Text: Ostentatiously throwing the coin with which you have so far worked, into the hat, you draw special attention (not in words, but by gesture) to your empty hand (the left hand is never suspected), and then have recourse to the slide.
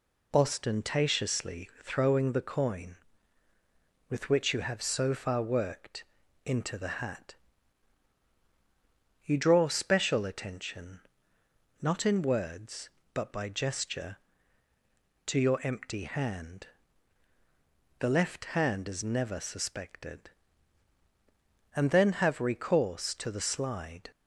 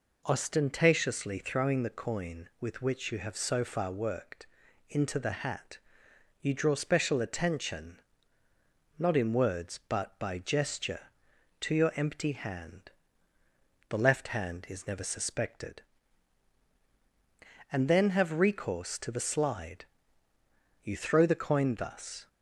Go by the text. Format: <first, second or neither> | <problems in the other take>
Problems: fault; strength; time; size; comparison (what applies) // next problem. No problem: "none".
first | goes on to say "You throw the coin thus"; from 20.8 s on; 1.4 s long